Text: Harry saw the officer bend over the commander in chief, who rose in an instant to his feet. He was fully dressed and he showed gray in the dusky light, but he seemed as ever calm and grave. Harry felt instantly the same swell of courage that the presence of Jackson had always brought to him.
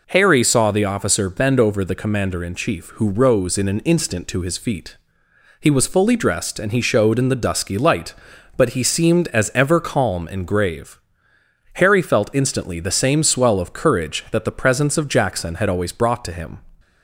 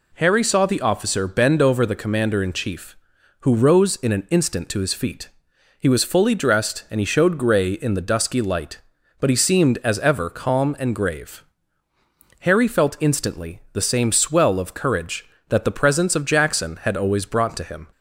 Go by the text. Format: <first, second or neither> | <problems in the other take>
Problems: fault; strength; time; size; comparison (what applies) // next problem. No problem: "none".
second | skips "gray"; at 7.1 s